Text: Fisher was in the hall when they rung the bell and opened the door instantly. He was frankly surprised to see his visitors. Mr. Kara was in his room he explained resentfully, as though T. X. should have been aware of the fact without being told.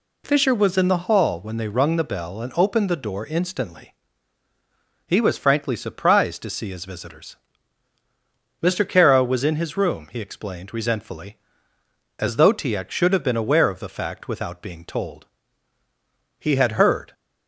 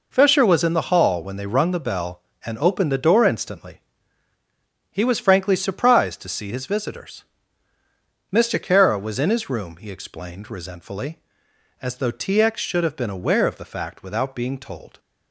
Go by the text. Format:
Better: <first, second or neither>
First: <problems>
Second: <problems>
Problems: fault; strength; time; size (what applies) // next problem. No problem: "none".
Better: second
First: goes on to say "He had heard"; noticeable; from 16.3 s on; 0.74 s long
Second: none